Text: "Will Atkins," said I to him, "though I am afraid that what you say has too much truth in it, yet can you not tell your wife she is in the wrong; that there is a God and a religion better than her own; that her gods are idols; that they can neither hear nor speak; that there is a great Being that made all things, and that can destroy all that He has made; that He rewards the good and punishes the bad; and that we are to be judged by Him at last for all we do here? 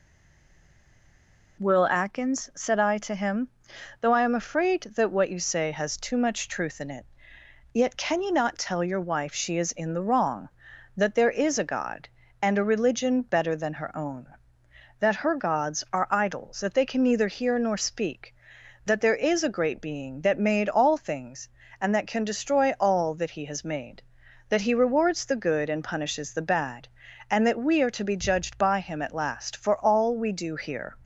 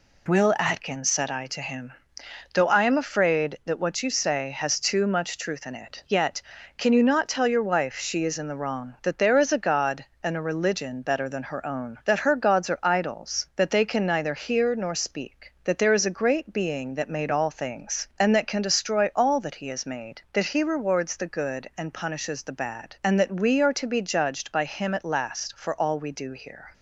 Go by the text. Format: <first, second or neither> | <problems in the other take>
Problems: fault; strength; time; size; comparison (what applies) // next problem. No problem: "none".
second | stays silent before the first word; noticeable; until 1.5 s; 1.5 s long